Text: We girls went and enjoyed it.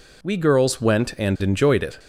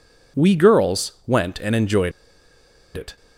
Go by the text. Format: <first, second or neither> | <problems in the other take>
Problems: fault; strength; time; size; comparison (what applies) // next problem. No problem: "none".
first | pauses between "enjoyed" and "it"; noticeable; at 2.1 s; 0.84 s long